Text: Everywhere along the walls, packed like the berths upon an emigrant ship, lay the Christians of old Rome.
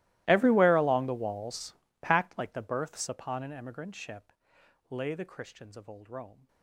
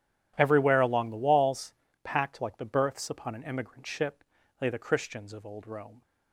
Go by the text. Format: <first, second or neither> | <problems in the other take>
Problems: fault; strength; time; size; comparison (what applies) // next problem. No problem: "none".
second | gets quieter; strong; throughout; 25.5 dB // starts louder than the rest; strong; until 1.2 s; 17.5 dB; strong in the second